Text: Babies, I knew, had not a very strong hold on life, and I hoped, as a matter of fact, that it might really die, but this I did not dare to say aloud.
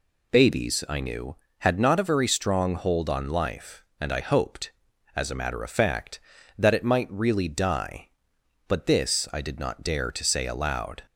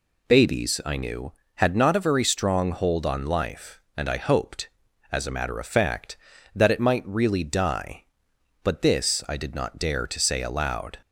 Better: neither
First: none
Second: none

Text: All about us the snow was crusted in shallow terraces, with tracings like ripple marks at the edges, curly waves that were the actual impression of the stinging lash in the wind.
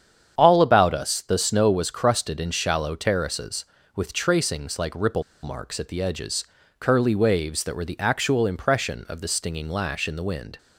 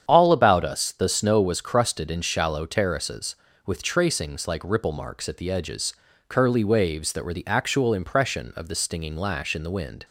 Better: second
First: starts louder than the rest; strong; until 1.3 s; 8.5 dB // pauses between "ripple" and "marks"; slight; at 5.2 s; 0.20 s long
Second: starts louder than the rest; strong; until 1.0 s; 8.5 dB

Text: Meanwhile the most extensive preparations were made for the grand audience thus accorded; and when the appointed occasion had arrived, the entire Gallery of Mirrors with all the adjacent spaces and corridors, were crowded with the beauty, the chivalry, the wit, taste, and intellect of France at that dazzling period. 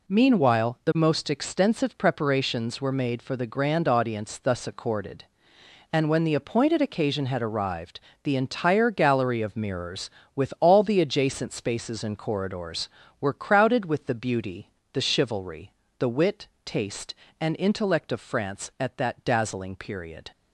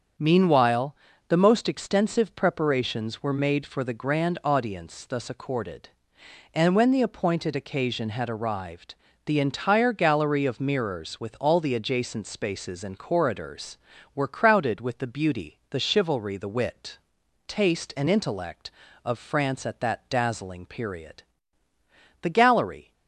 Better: first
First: none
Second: starts louder than the rest; strong; until 1.5 s; 7.5 dB // pauses between "Meanwhile" and "the"; slight; at 0.9 s; 0.34 s long // goes on to say "The gallery"; noticeable; from 22.2 s on; 0.72 s long

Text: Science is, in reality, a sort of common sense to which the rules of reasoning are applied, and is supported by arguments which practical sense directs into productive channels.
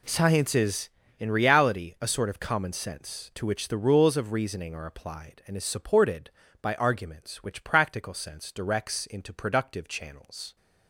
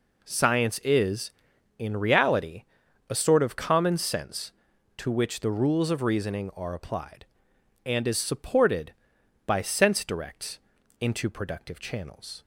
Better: first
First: none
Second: skips "arguments which practical"; at 9.6 s // pauses between "directs" and "into"; at 10.5 s; 0.42 s long

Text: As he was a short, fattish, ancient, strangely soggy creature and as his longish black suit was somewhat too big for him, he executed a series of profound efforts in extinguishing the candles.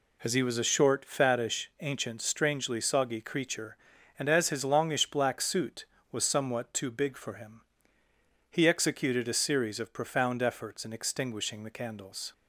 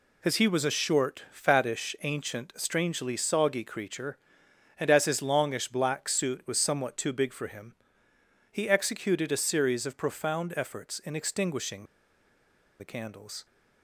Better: first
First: none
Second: pauses between "extinguishing" and "the"; noticeable; at 11.8 s; 0.96 s long

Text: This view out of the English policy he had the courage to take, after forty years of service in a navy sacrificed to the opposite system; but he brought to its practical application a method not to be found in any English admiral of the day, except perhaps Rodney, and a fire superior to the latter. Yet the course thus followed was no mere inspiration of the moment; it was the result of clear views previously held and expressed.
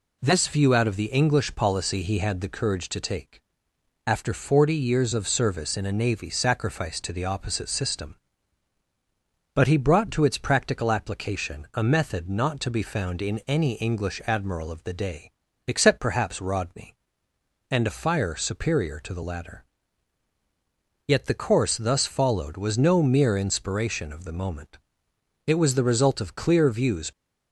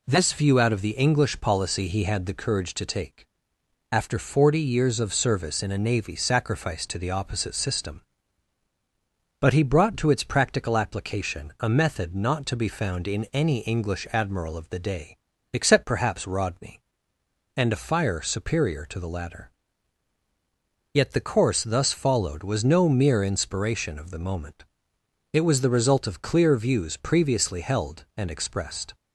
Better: second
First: stops before "previously held and expressed"; at 27.1 s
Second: none

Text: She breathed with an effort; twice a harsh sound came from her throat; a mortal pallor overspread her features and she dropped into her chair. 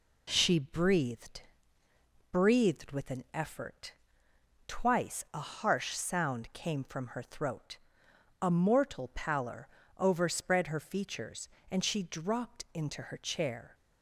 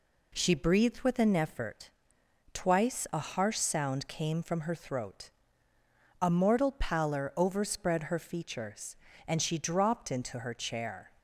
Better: second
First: says "breathed" twice; at 2.3 s // pauses between "pallor" and "overspread"; slight; at 9.6 s; 0.28 s long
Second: none

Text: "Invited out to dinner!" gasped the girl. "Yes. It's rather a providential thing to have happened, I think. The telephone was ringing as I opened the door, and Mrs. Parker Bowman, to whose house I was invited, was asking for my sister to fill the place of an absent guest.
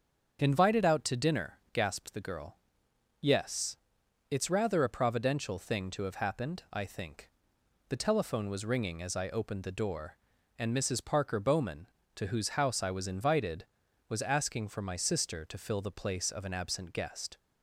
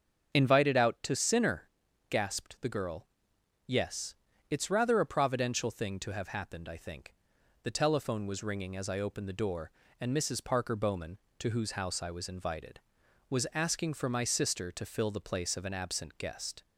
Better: first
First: starts louder than the rest; until 1.4 s; 7 dB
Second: starts louder than the rest; until 1.3 s; 7 dB // says "sinner" for "dinner"; at 1.1 s

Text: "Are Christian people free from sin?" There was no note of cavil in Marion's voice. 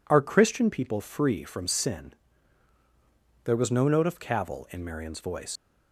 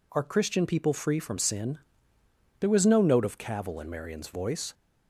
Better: second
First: leaves "voice" unfinished; at 5.5 s; 115 ms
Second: none

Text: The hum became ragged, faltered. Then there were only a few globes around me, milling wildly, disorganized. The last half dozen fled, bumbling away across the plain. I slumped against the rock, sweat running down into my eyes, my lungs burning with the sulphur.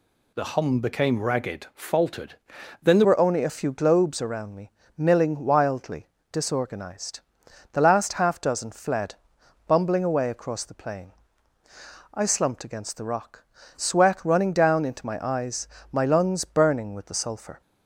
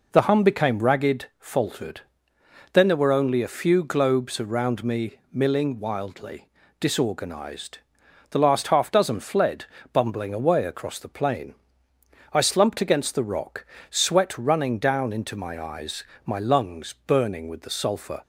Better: second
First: changes voice at "were"; from 3.0 s on; 14.6 s long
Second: none

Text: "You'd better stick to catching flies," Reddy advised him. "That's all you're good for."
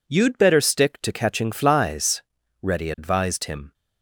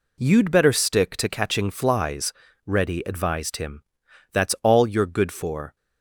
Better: second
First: stops before "That's all you're good for"; at 3.7 s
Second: none

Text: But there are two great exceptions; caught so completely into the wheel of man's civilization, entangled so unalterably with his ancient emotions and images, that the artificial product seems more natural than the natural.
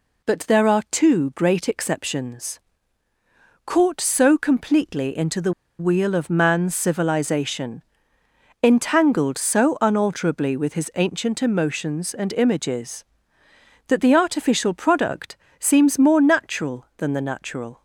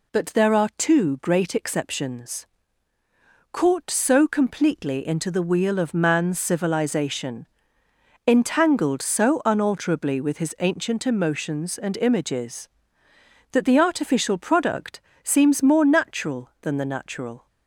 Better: second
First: pauses between "the" and "wheel"; slight; at 5.5 s; 0.28 s long // pauses between "product" and "seems"; slight; at 15.3 s; 0.24 s long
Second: pauses between "product" and "seems"; slight; at 15.0 s; 0.24 s long

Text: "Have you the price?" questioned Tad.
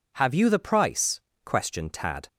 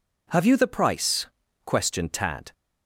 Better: neither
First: none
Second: none

